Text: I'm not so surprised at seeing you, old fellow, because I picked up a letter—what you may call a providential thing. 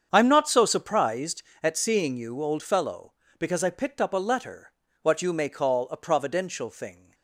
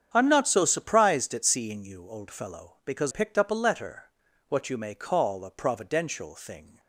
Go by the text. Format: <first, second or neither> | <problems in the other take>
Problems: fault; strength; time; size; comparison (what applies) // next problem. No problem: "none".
first | starts louder than the rest; strong; until 1.1 s; 8 dB; strong in the first // skips "I"; at 3.1 s